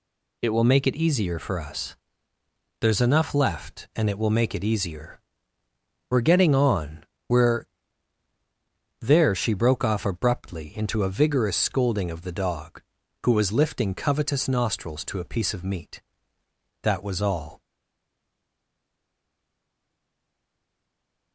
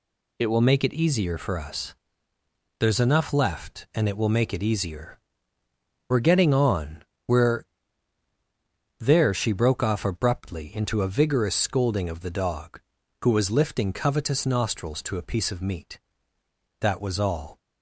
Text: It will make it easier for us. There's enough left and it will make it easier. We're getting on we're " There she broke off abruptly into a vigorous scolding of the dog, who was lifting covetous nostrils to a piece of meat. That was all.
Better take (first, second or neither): second